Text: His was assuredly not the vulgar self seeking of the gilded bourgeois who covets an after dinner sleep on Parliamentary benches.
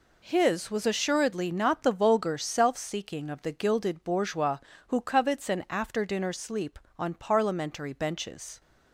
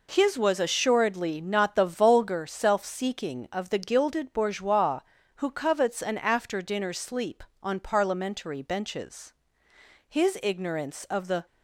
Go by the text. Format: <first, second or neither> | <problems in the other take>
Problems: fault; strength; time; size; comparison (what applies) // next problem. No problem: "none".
first | goes on to say "His ignorance of the"; from 10.0 s on; 1.3 s long